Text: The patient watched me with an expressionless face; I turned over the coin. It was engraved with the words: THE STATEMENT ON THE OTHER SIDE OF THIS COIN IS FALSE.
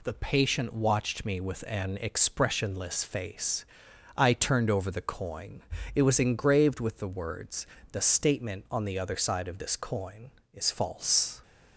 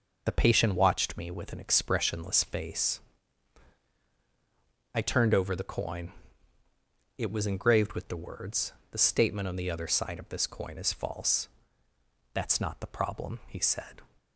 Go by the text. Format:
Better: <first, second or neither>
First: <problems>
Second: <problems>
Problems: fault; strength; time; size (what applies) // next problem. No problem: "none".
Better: first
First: none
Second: goes on to say "That's not the problem he said"; strong; from 12.3 s on; 1.6 s long